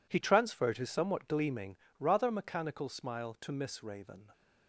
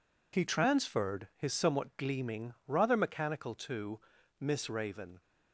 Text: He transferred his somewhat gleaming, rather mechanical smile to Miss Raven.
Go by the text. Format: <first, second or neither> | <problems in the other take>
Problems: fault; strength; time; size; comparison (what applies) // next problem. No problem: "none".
first | skips "smile"; at 3.5 s // pauses between "to" and "Miss"; at 3.9 s; 0.40 s long